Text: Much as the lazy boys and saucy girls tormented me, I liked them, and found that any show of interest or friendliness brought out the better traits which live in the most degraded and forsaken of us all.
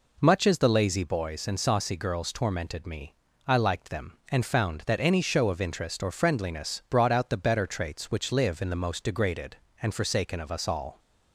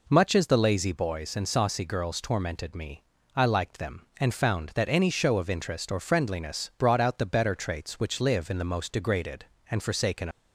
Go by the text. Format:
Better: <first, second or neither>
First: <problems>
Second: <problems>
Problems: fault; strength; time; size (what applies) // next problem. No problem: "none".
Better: first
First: none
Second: stops before "of us all"; at 10.3 s